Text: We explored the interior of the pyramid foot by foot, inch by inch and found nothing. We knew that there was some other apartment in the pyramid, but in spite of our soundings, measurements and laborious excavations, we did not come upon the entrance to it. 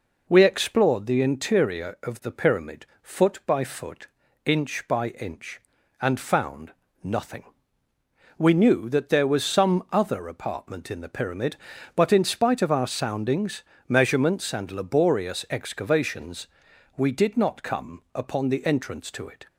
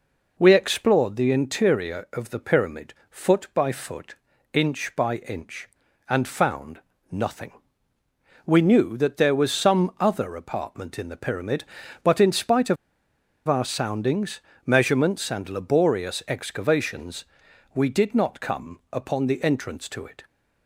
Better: first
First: pauses between "pyramid" and "foot"; slight; at 2.8 s; 0.16 s long // pauses between "found" and "nothing"; slight; at 6.7 s; 0.32 s long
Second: pauses between "pyramid" and "foot"; slight; at 2.9 s; 0.16 s long // pauses between "found" and "nothing"; slight; at 6.7 s; 0.32 s long // pauses between "of" and "our"; noticeable; at 12.7 s; 0.72 s long

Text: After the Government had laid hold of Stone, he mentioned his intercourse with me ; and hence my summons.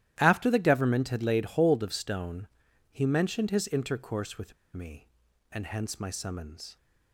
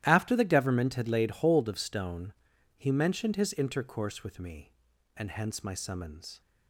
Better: second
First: starts louder than the rest; strong; until 1.1 s; 13 dB // pauses between "with" and "me"; slight; at 4.5 s; 0.21 s long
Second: starts louder than the rest; strong; until 1.0 s; 13 dB

